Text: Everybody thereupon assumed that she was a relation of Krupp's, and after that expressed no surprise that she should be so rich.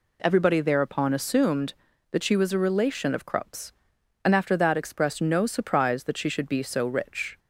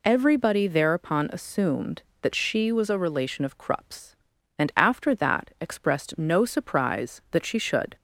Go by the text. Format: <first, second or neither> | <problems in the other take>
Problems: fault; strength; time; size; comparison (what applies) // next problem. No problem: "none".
first | stops before "be so rich"; at 7.9 s